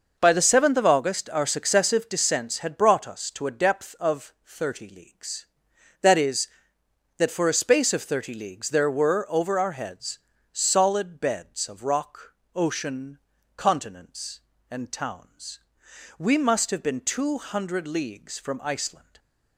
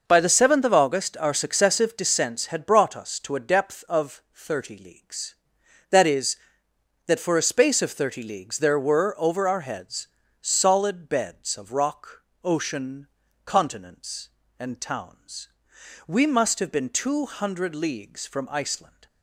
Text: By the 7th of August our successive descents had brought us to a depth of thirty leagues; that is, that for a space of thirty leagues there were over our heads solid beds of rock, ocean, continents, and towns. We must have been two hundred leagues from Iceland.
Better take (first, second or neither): neither